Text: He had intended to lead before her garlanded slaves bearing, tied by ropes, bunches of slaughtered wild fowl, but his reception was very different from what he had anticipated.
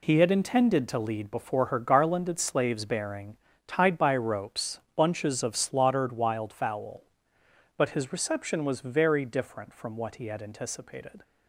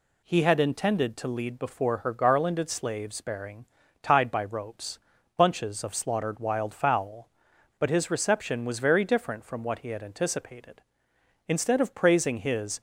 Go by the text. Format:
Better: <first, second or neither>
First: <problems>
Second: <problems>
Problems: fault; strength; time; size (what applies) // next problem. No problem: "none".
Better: first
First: none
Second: goes on to say "Instead of praising his"; from 11.4 s on; 1.3 s long